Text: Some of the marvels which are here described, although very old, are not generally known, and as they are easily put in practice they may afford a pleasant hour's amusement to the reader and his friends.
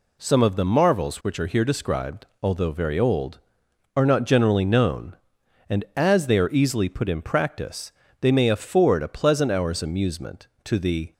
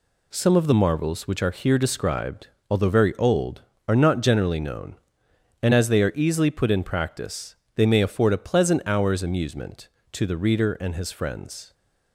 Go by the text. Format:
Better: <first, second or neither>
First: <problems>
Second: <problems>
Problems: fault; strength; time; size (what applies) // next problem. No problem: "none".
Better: second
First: pauses between "practice" and "they"; slight; at 7.9 s; 0.30 s long // stops before "reader and his friends"; at 11.1 s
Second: pauses between "practice" and "they"; slight; at 7.5 s; 0.22 s long